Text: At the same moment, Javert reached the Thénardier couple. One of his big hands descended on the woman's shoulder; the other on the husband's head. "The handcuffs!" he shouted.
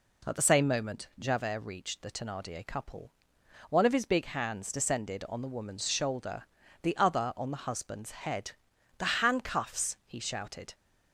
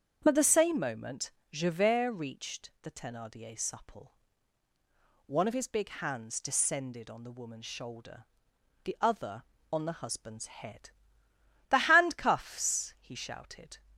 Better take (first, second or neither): first